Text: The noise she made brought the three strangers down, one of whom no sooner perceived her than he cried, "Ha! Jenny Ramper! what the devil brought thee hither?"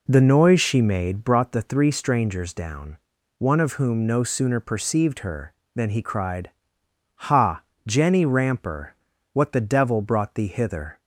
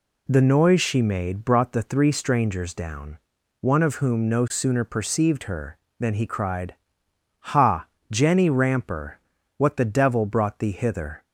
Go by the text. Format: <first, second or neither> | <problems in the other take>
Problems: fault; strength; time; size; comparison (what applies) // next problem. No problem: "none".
second | starts louder than the rest; until 1.3 s; 4 dB